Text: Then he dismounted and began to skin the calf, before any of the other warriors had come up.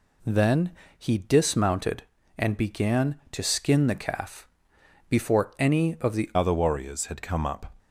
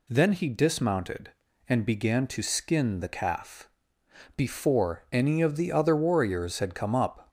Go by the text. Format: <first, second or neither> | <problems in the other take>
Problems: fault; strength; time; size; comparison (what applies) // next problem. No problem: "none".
second | pauses between "Then" and "he"; slight; at 0.7 s; 0.26 s long // changes voice at "other"; from 6.3 s on; 1.4 s long